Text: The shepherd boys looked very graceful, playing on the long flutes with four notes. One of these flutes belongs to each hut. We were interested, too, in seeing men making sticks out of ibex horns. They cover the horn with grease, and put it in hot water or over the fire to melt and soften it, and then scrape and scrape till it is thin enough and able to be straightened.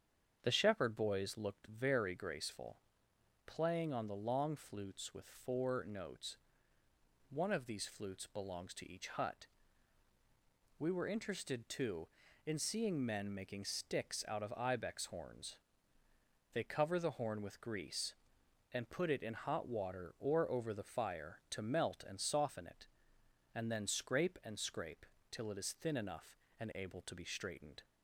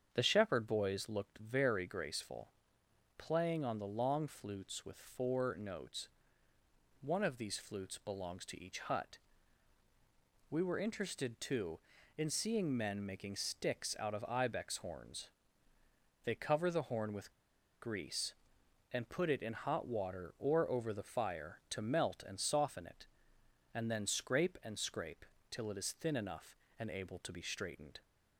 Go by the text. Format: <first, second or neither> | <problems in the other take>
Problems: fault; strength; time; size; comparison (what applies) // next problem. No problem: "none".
first | starts louder than the rest; strong; until 1.1 s; 7.5 dB; strong in the first // pauses between "with" and "grease"; noticeable; at 17.3 s; 0.50 s long // pauses between "scrape" and "till"; slight; at 25.2 s; 0.26 s long; slight in the first